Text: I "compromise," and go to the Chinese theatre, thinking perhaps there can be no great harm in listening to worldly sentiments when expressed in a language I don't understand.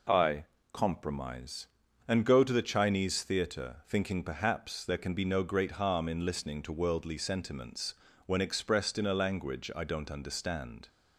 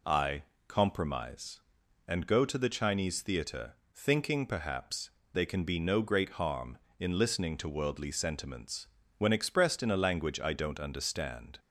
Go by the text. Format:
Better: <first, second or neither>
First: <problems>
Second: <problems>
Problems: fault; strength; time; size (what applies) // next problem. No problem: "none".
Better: first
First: pauses between "I" and "compromise"; slight; at 0.4 s; 0.26 s long // pauses between "sentiments" and "when"; slight; at 7.9 s; 0.32 s long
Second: pauses between "I" and "compromise"; slight; at 0.4 s; 0.24 s long // says "they" for "there"; at 5.3 s // pauses between "sentiments" and "when"; slight; at 8.8 s; 0.32 s long